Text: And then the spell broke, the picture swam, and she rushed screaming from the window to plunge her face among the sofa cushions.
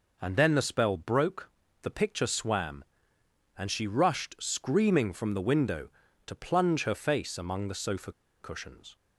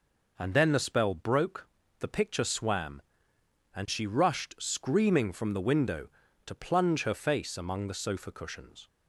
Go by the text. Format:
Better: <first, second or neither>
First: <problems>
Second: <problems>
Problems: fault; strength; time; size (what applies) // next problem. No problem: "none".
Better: second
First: pauses between "sofa" and "cushions"; slight; at 8.1 s; 0.29 s long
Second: none